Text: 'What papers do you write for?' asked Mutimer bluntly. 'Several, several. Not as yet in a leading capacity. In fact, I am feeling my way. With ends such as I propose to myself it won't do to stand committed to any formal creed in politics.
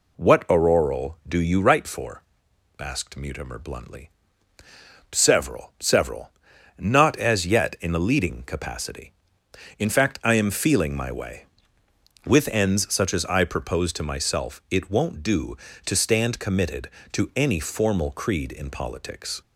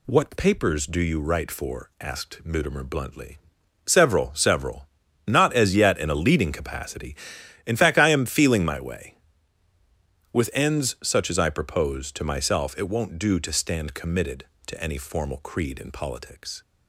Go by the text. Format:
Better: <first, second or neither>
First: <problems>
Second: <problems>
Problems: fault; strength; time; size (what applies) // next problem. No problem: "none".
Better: second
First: says "auroral" for "papers"; at 0.4 s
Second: none